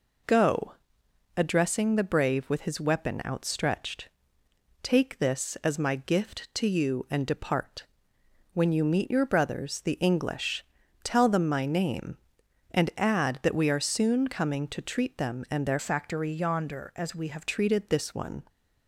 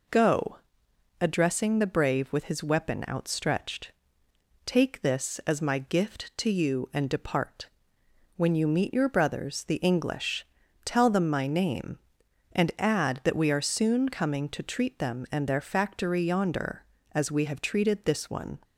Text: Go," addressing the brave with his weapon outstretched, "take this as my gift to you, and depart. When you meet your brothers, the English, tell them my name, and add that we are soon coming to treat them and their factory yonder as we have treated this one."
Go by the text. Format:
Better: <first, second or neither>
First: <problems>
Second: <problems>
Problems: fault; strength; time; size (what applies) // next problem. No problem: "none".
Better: second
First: changes voice from "factory" to "have"; from 15.7 to 17.4 s; 1.7 s long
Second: none